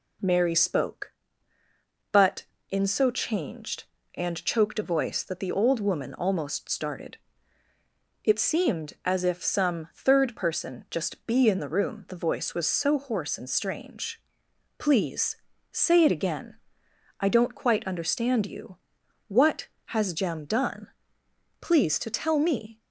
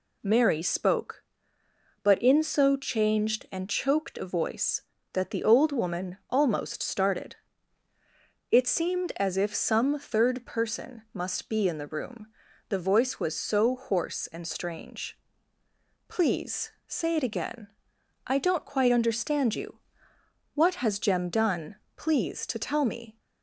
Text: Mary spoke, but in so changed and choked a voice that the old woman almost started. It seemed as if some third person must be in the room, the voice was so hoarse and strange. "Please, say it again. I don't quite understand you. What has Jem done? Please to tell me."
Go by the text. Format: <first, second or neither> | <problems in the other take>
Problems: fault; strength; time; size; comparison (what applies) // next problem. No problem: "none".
second | says "just" for "must"; at 10.9 s